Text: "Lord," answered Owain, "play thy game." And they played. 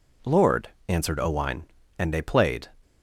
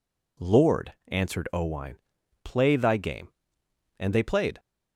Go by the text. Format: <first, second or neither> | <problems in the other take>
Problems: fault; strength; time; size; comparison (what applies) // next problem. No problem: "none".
second | skips "play thy game"; at 1.8 s